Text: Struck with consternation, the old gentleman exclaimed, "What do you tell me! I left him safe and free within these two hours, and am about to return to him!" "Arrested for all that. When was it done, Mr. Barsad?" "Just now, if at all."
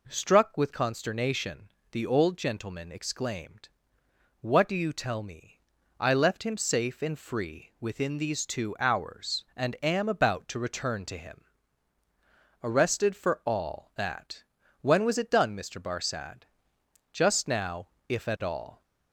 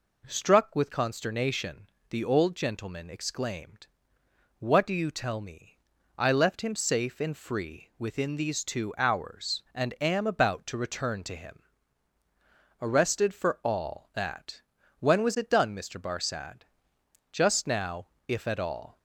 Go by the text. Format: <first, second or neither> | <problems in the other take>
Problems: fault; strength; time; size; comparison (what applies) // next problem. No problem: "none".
neither | none